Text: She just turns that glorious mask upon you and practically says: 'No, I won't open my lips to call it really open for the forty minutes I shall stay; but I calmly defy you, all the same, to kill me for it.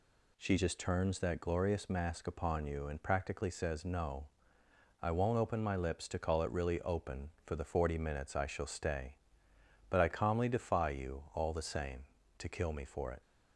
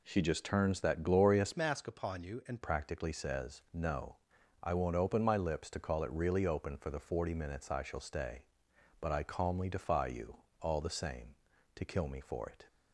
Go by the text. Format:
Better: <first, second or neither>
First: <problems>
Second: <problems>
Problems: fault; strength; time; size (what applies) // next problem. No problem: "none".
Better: first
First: none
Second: changes voice from "mask" to "and"; from 1.5 to 2.6 s; 1.1 s long